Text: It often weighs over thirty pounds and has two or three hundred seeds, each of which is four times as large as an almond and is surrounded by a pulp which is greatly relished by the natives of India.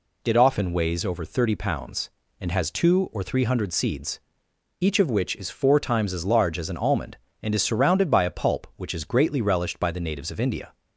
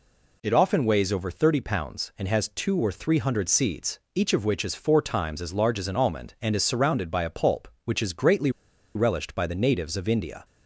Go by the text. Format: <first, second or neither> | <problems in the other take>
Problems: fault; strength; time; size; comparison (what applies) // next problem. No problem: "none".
first | pauses between "greatly" and "relished"; at 8.4 s; 0.45 s long